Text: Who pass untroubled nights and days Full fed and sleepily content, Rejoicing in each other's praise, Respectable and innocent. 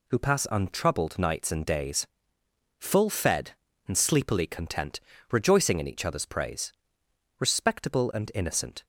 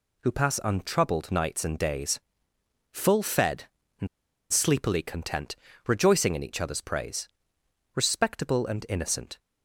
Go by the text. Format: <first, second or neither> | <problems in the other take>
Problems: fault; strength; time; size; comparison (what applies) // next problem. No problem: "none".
first | pauses between "days" and "Full"; noticeable; at 2.1 s; 0.72 s long; noticeable in the first // pauses between "and" and "sleepily"; at 4.0 s; 0.44 s long